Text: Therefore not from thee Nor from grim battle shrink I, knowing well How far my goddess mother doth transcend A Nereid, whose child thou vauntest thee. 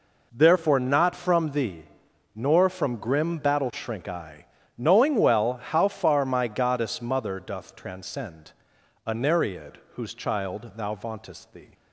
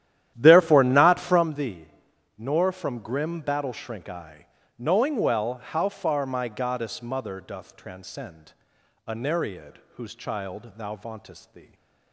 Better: first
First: pauses between "thee" and "Nor"; noticeable; at 1.8 s; 0.52 s long // pauses between "transcend" and "A"; noticeable; at 8.5 s; 0.52 s long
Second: starts louder than the rest; strong; until 1.5 s; 11.5 dB // pauses between "thee" and "Nor"; noticeable; at 1.8 s; 0.52 s long // pauses between "transcend" and "A"; noticeable; at 8.5 s; 0.52 s long

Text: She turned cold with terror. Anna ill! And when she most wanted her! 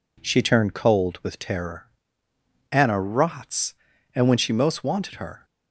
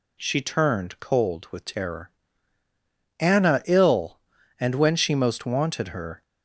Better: second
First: says "rots" for "ill"; at 3.0 s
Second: none

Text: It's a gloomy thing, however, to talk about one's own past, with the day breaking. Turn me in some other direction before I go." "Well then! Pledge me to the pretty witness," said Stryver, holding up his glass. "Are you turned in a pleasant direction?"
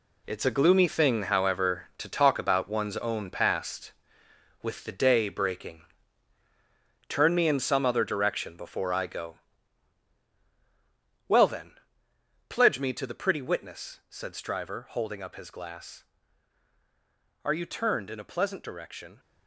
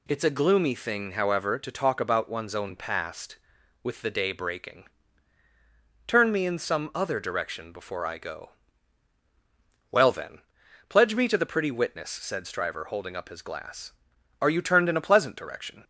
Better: second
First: gets quieter; strong; throughout; 10 dB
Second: none

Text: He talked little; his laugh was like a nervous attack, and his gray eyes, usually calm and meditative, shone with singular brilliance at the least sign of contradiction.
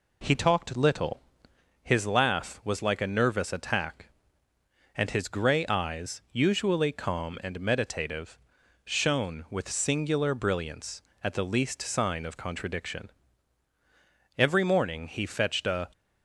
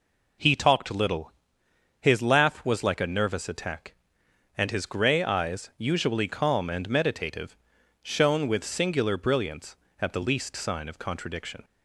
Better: second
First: goes on to say "Every morning he fetched a"; from 14.3 s on; 1.5 s long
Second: none

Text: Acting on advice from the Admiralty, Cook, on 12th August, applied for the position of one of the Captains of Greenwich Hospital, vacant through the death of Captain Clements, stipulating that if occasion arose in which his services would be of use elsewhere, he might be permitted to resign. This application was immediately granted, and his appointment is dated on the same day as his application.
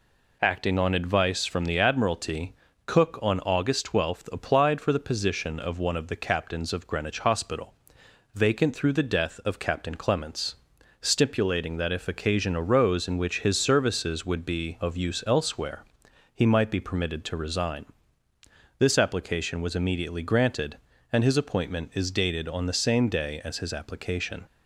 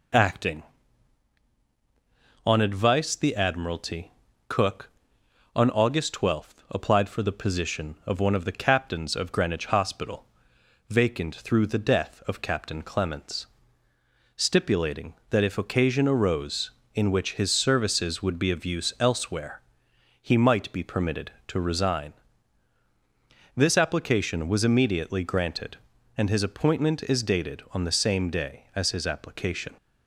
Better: first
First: none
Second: skips "from"; at 3.1 s

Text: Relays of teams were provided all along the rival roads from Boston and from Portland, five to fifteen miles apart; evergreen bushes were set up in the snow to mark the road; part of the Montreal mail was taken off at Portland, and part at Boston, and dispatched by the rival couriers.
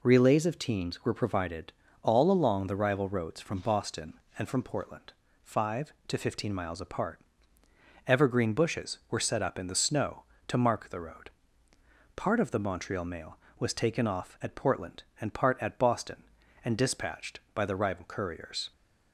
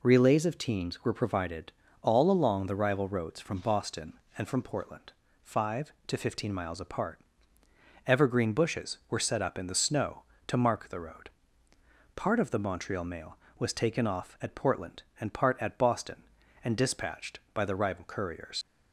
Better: first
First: pauses between "provided" and "all"; slight; at 1.7 s; 0.30 s long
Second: pauses between "provided" and "all"; slight; at 1.7 s; 0.30 s long // leaves "couriers" unfinished; at 18.6 s; 100 ms

